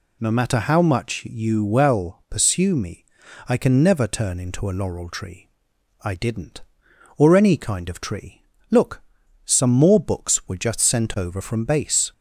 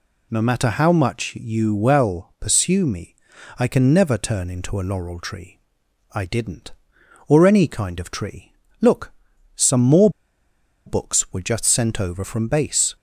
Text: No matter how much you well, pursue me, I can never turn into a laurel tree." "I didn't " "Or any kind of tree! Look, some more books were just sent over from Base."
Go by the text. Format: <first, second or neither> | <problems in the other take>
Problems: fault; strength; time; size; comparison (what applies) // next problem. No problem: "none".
first | pauses between "more" and "books"; noticeable; at 10.0 s; 0.77 s long